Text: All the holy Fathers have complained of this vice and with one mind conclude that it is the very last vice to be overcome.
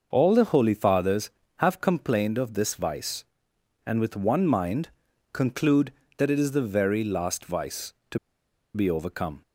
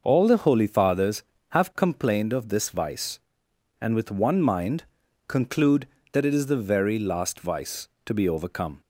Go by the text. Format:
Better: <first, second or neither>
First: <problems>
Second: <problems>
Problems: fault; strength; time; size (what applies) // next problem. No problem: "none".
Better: second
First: starts louder than the rest; noticeable; until 1.1 s; 6 dB // pauses between "mind" and "conclude"; at 4.8 s; 0.42 s long // pauses between "to" and "be"; noticeable; at 8.1 s; 0.57 s long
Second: starts louder than the rest; noticeable; until 1.0 s; 6 dB // pauses between "mind" and "conclude"; at 4.8 s; 0.42 s long